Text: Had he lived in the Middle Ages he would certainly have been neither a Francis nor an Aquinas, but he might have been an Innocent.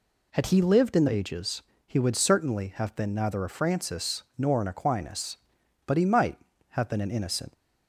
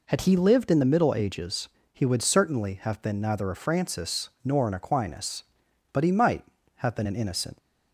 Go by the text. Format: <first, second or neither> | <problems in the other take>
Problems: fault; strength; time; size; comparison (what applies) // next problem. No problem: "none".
second | skips "Middle"; at 1.0 s // pauses between "Ages" and "he"; slight; at 1.6 s; 0.26 s long; slight in the second